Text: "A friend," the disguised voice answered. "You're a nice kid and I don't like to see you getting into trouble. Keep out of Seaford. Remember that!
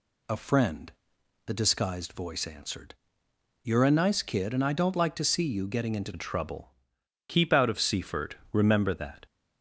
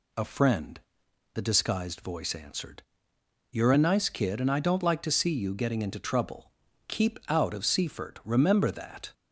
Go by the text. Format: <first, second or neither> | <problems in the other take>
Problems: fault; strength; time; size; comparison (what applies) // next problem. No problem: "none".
second | changes voice at "trouble"; from 6.1 s on; 3.1 s long